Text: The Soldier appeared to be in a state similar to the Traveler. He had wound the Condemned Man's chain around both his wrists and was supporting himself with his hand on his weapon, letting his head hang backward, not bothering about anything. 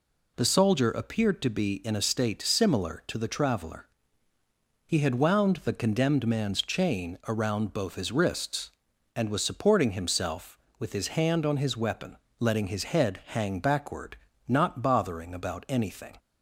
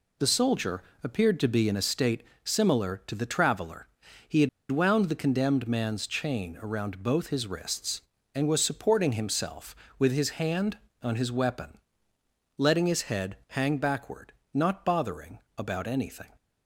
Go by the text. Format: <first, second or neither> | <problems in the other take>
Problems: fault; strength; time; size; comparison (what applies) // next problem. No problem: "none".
first | pauses between "Soldier" and "appeared"; slight; at 0.8 s; 0.22 s long // pauses between "state" and "similar"; slight; at 2.2 s; 0.20 s long // pauses between "had" and "wound"; slight; at 4.4 s; 0.22 s long // pauses between "bothering" and "about"; slight; at 15.3 s; 0.18 s long